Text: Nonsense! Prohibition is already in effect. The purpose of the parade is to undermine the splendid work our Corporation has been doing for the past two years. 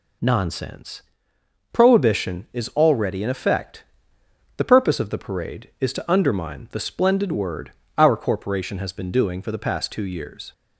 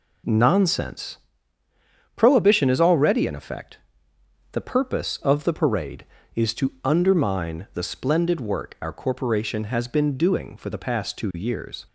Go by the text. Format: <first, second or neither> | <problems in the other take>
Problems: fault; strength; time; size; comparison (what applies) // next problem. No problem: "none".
second | says "word" for "work"; at 7.3 s